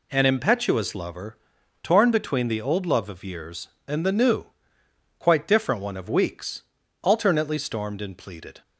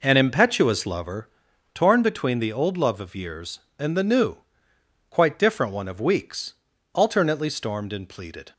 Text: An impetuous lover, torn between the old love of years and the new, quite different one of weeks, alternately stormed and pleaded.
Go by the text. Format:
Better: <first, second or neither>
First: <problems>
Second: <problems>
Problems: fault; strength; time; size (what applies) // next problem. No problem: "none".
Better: first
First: none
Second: starts louder than the rest; noticeable; until 1.4 s; 4.5 dB